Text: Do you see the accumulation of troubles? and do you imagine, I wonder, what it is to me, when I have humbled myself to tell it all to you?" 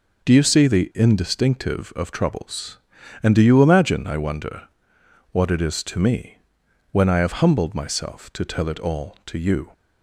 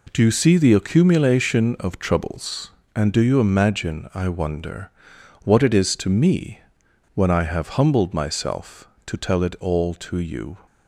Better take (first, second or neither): second